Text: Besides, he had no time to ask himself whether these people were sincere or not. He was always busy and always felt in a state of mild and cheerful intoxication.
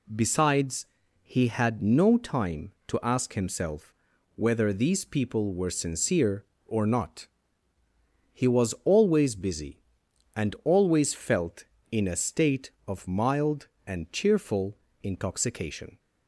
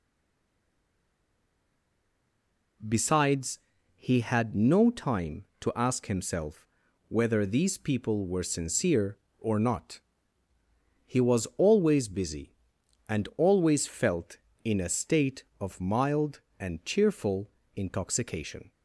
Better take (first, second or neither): first